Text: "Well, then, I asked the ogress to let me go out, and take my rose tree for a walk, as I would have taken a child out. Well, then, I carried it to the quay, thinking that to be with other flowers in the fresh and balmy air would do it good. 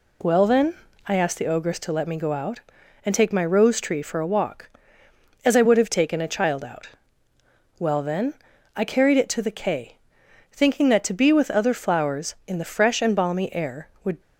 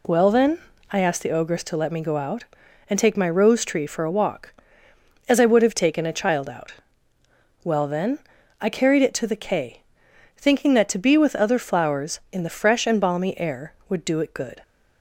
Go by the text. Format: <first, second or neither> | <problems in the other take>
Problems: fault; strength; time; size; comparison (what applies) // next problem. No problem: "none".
second | stops before "do it good"; at 14.2 s